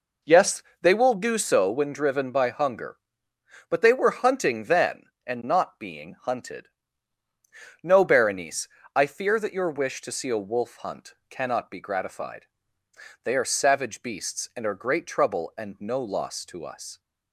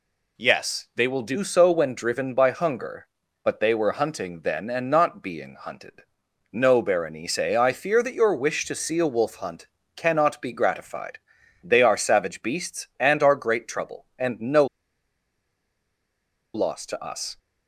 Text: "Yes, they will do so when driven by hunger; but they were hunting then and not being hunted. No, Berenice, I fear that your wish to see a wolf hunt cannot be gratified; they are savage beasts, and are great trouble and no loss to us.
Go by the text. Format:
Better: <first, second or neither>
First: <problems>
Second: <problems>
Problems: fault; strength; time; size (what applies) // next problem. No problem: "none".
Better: first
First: none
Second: pauses between "hunt" and "cannot"; slight; at 9.6 s; 0.28 s long // pauses between "no" and "loss"; strong; at 14.6 s; 1.8 s long